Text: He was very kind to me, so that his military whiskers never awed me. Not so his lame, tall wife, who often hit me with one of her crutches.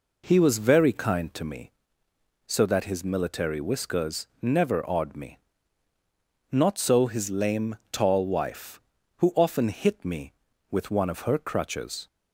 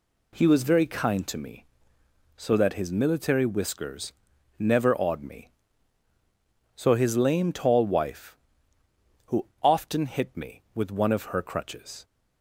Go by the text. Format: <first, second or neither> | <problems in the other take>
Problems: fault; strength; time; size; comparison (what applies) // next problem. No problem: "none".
first | pauses between "whiskers" and "never"; noticeable; at 4.1 s; 0.46 s long // skips "Not"; at 6.1 s // pauses between "who" and "often"; slight; at 9.4 s; 0.16 s long